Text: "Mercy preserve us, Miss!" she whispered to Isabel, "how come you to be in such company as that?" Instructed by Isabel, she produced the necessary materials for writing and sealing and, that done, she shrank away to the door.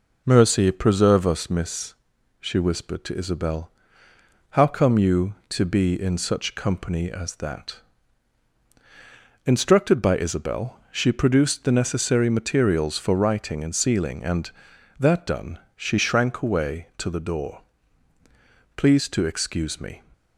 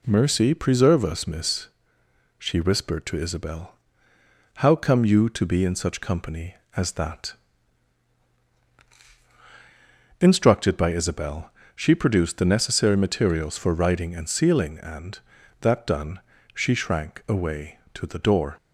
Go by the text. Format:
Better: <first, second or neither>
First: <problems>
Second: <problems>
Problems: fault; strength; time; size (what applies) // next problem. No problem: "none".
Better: second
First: goes on to say "Please to excuse me"; noticeable; from 18.7 s on; 1.2 s long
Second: none